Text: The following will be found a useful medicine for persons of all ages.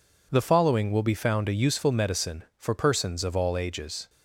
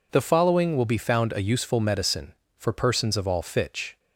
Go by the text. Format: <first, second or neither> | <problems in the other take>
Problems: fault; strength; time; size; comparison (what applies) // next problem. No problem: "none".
first | says "fitch" for "ages"; at 3.4 s